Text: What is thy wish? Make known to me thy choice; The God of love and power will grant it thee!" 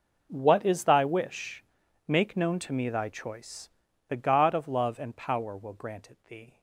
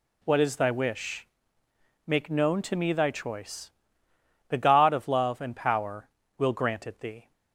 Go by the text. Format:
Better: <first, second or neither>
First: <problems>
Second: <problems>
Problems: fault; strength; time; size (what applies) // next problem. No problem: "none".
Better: second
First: gets quieter; strong; throughout; 17.5 dB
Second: none